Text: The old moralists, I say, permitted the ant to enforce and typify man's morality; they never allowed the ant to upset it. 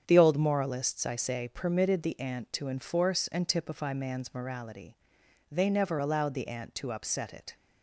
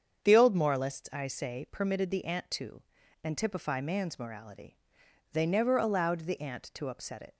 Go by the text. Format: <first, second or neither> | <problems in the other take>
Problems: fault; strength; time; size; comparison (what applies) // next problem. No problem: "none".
first | starts louder than the rest; strong; until 1.2 s; 7.5 dB; strong in the first // skips "enforce"; at 3.0 s